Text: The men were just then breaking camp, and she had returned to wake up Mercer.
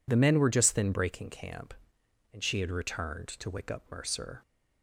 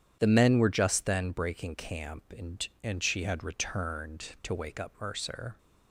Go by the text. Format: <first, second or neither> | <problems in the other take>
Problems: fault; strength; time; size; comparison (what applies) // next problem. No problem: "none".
first | starts louder than the rest; strong; until 1.2 s; 9.5 dB // says "and" twice; at 2.8 s